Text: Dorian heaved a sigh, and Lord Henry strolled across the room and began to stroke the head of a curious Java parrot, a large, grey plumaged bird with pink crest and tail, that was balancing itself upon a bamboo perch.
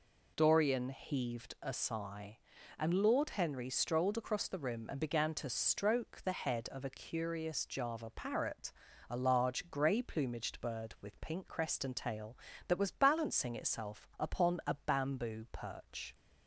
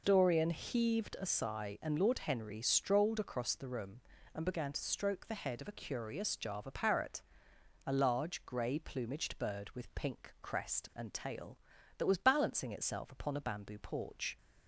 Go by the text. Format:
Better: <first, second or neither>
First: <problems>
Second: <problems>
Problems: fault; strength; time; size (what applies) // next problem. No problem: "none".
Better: first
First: none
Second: says "porch" for "perch"; at 13.7 s